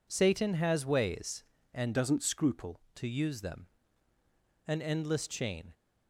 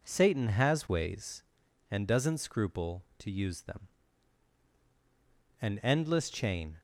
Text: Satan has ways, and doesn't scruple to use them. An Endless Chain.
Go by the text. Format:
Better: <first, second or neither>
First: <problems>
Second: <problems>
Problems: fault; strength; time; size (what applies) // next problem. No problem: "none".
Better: second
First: changes voice from "doesn't" to "scruple"; from 1.9 to 2.7 s; 0.8 s long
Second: none